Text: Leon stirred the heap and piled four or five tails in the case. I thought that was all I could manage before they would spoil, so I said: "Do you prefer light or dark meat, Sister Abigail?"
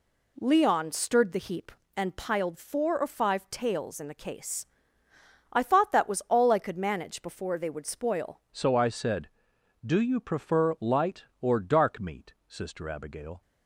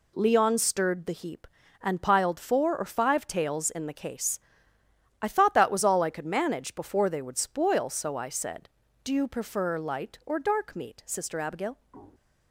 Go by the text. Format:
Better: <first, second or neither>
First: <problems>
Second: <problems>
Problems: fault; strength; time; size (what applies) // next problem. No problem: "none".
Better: second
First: changes voice at "so"; from 8.5 s on; 4.9 s long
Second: none